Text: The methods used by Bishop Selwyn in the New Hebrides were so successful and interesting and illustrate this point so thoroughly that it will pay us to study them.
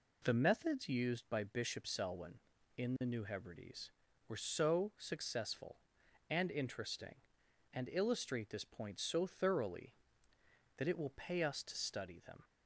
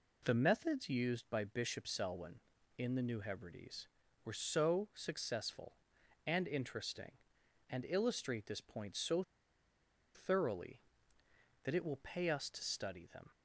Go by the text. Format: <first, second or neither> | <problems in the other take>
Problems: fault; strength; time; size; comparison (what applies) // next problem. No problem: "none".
first | pauses between "so" and "thoroughly"; noticeable; at 9.2 s; 0.93 s long